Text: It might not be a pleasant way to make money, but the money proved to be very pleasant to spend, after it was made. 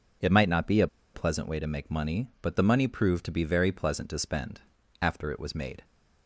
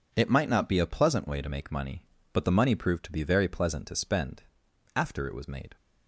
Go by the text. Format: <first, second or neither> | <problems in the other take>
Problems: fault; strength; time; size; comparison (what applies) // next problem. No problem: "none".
second | pauses between "a" and "pleasant"; slight; at 0.8 s; 0.27 s long